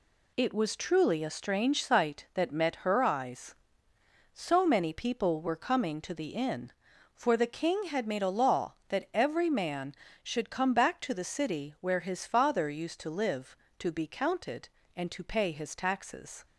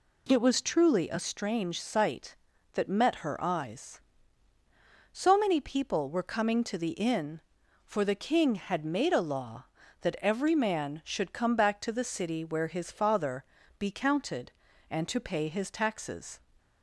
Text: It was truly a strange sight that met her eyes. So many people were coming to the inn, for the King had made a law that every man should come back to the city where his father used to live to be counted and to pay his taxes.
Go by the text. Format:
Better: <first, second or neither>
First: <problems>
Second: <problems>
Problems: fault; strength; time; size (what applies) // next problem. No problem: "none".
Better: first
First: none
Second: skips "used to live to"; at 13.6 s